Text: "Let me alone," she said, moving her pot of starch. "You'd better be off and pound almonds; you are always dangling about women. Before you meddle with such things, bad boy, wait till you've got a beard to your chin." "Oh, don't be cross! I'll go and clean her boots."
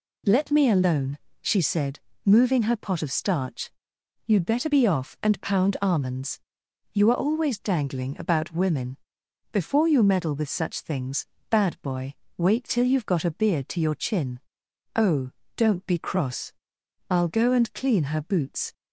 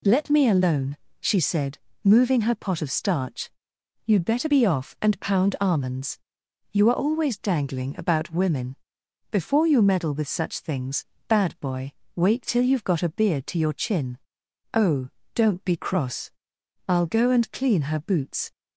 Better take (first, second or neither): neither